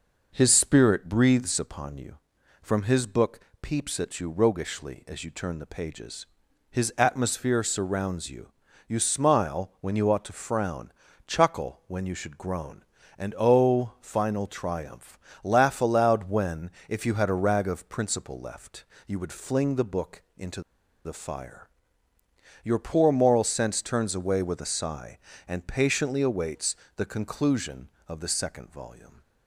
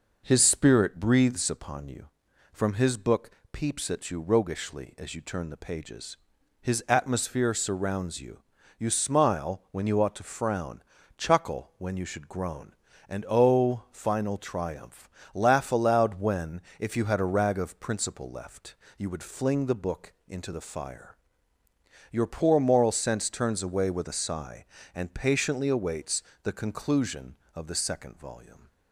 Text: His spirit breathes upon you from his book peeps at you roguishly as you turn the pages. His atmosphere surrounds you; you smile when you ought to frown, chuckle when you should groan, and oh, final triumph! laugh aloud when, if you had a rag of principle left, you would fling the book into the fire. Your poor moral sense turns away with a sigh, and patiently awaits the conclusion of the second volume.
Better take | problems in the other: second | pauses between "book" and "peeps"; slight; at 3.3 s; 0.24 s long; slight in the second // pauses between "into" and "the"; at 20.5 s; 0.45 s long // pauses between "awaits" and "the"; slight; at 26.7 s; 0.20 s long; slight in the second

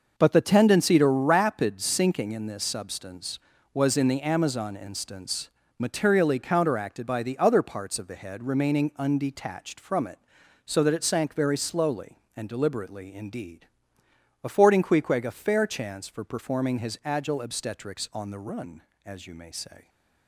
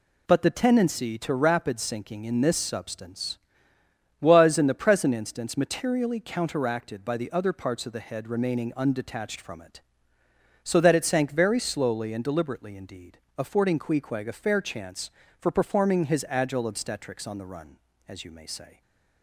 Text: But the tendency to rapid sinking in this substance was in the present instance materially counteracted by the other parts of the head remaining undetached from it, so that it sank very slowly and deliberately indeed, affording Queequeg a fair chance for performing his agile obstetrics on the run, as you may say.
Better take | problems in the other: second | says "amazon" for "present"; at 4.2 s // pauses between "instance" and "materially"; slight; at 5.5 s; 0.28 s long

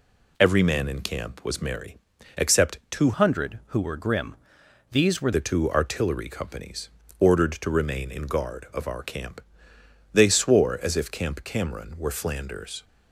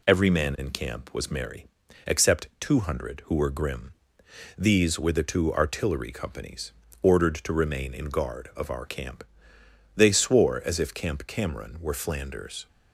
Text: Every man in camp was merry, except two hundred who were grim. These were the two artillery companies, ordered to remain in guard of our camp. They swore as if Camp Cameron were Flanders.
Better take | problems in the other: second | changes voice from "hundred" to "were"; from 3.1 to 5.3 s; 2.2 s long

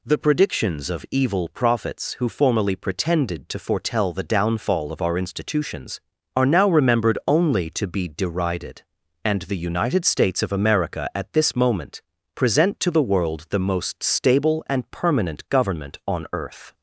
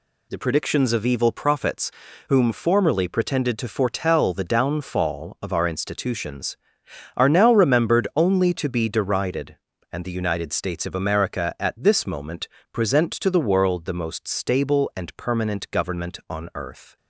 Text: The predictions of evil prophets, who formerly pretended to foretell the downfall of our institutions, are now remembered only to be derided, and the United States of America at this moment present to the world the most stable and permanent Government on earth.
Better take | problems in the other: first | says "whom" for "who"; at 2.2 s // pauses between "moment" and "present"; slight; at 12.4 s; 0.24 s long; slight in the first

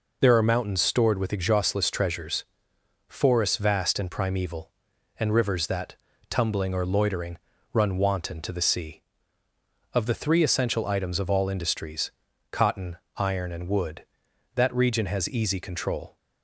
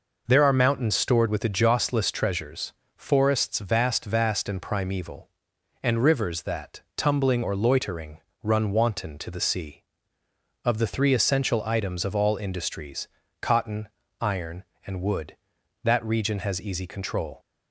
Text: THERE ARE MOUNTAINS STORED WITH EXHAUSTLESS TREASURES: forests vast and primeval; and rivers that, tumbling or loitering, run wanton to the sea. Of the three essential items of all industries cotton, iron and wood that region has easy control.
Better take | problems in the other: first | says "vast" twice; at 4.0 s // pauses between "industries" and "cotton"; slight; at 13.0 s; 0.34 s long; also in the first

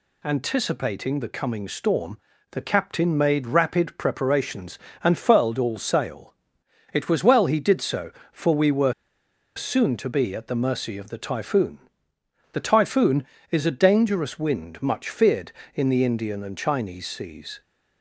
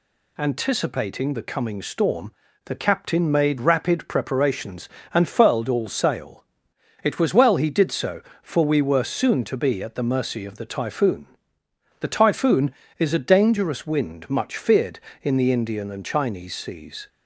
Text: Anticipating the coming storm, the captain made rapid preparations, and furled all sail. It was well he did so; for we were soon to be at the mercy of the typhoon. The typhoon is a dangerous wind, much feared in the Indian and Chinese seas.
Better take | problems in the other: second | pauses between "were" and "soon"; noticeable; at 8.9 s; 0.63 s long

